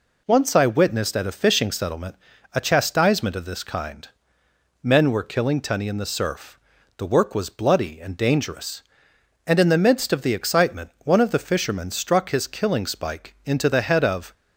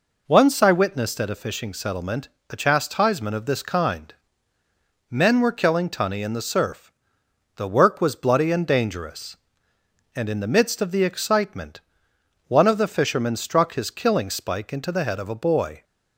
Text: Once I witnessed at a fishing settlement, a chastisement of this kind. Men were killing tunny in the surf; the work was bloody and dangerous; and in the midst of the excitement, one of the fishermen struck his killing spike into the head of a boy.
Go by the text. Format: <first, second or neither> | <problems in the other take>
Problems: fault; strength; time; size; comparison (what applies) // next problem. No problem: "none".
second | stops before "a boy"; at 14.3 s